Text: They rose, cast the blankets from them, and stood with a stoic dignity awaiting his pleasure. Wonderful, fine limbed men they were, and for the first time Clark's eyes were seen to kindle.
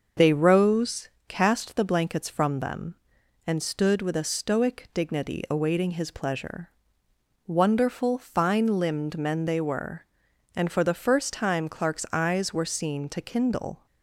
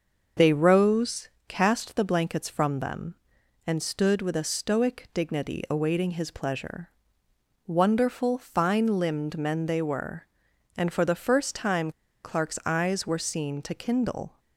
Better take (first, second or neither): first